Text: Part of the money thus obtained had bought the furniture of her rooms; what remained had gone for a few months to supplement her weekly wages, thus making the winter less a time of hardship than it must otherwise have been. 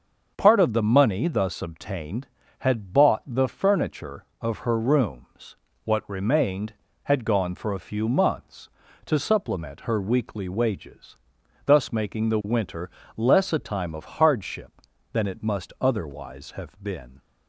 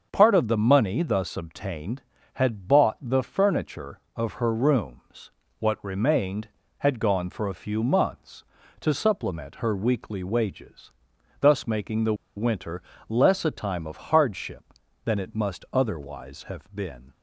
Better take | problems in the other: first | starts louder than the rest; until 1.1 s; 6.5 dB; also in the first // pauses between "the" and "winter"; slight; at 12.1 s; 0.22 s long // pauses between "winter" and "less"; slight; at 12.8 s; 0.26 s long; slight in the first

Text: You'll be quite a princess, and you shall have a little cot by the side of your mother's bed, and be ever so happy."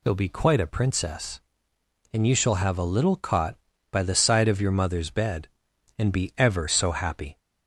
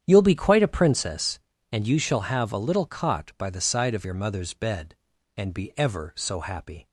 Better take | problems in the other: first | starts louder than the rest; strong; until 1.1 s; 9 dB

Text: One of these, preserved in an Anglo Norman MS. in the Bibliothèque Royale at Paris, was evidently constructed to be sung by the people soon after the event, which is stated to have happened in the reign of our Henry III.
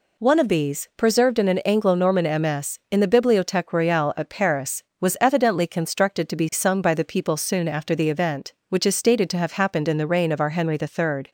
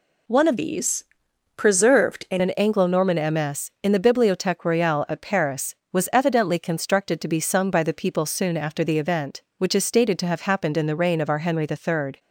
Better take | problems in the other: first | changes voice from "these" to "in"; from 0.5 to 2.4 s; 1.9 s long

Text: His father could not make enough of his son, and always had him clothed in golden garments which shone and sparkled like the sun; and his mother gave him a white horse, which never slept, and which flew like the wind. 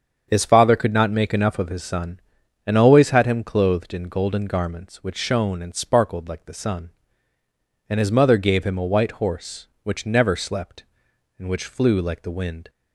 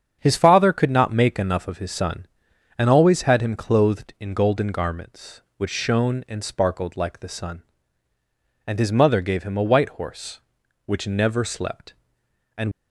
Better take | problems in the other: first | starts louder than the rest; strong; until 1.2 s; 7.5 dB; strong in the first // stops before "which flew like the wind"; at 12.7 s

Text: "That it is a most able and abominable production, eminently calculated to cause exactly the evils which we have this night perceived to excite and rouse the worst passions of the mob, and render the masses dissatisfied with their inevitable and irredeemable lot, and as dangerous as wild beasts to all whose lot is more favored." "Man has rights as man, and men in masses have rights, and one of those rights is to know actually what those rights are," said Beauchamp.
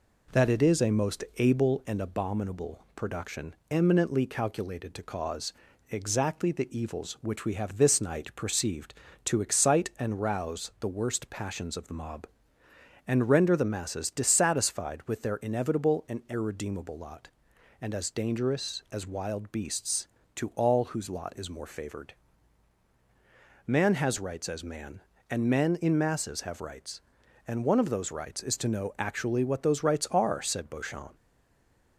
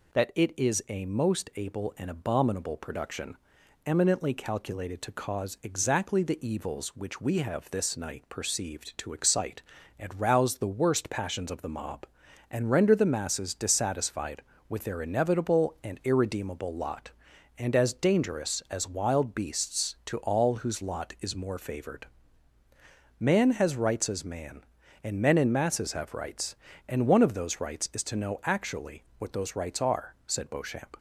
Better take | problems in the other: second | pauses between "cause" and "exactly"; slight; at 5.5 s; 0.36 s long // stays silent after the last word; slight; from 31.1 s on; 0.8 s long

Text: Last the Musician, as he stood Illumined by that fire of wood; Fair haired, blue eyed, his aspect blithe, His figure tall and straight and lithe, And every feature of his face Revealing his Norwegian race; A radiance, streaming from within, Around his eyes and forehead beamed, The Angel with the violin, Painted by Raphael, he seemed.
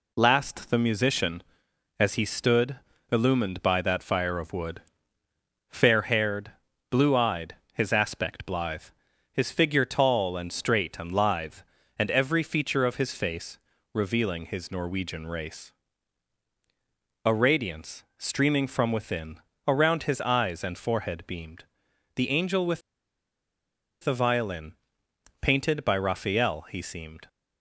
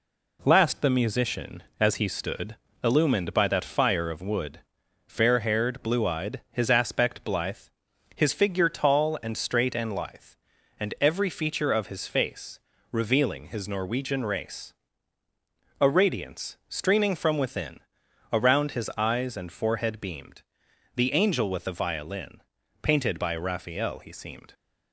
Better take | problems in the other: second | pauses between "stood" and "Illumined"; slight; at 2.7 s; 0.34 s long; slight in the second // pauses between "face" and "Revealing"; slight; at 13.5 s; 0.34 s long; slight in the second // pauses between "with" and "the"; at 22.8 s; 1.2 s long

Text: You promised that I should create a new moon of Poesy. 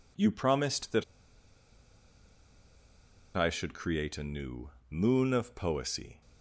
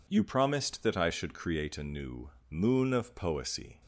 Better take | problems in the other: second | pauses between "that" and "I"; strong; at 1.0 s; 2.3 s long // pauses between "new" and "moon"; slight; at 4.7 s; 0.18 s long; slight in the second

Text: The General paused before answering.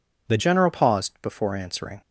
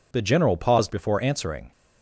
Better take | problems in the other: second | changes voice at "General"; from 0.3 s on; 1.7 s long

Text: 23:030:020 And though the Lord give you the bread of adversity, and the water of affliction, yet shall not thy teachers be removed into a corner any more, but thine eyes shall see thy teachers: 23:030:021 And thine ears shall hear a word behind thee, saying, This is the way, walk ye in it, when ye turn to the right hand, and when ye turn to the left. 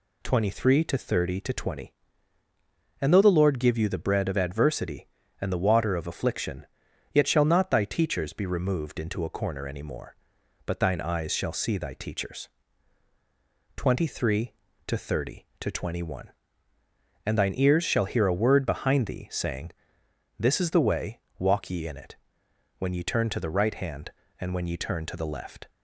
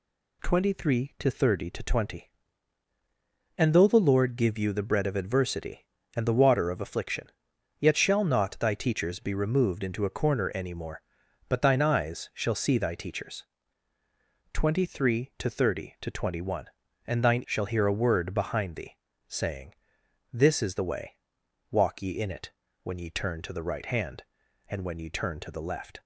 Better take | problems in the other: first | skips "ears"; at 17.4 s

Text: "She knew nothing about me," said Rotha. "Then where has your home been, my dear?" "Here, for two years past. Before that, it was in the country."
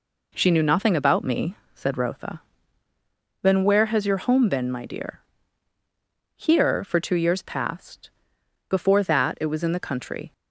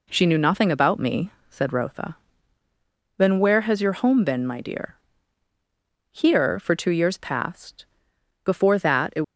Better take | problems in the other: first | stops before "was in the country"; at 9.2 s

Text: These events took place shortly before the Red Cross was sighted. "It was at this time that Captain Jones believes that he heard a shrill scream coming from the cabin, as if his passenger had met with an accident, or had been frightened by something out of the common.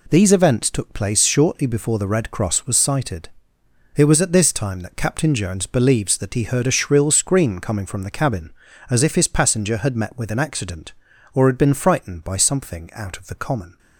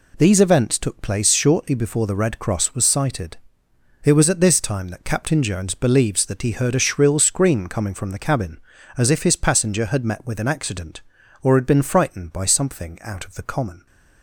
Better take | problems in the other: neither | none

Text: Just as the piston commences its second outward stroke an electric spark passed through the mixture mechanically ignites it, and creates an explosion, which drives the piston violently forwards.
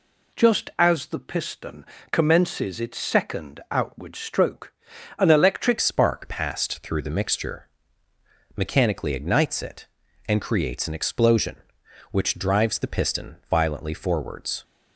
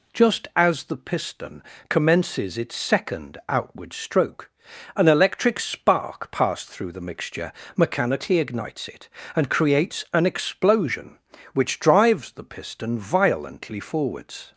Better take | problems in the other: second | pauses between "piston" and "commences"; slight; at 1.8 s; 0.26 s long; slight in the second // pauses between "stroke" and "an"; noticeable; at 4.7 s; 0.46 s long; noticeable in the second // changes voice at "spark"; from 5.8 s on; 8.8 s long // pauses between "mixture" and "mechanically"; noticeable; at 7.6 s; 0.88 s long; slight in the second // pauses between "piston" and "violently"; slight; at 13.3 s; 0.16 s long

